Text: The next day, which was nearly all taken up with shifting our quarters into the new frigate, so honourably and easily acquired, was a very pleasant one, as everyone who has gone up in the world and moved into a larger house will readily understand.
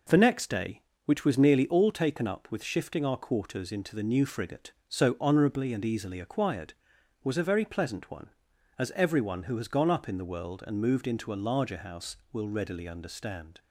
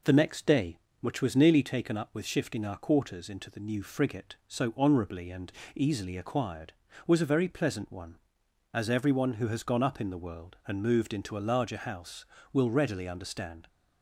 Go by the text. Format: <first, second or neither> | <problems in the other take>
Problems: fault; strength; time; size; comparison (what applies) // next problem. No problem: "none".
first | skips "all"; at 1.6 s // pauses between "and" and "easily"; slight; at 5.4 s; 0.28 s long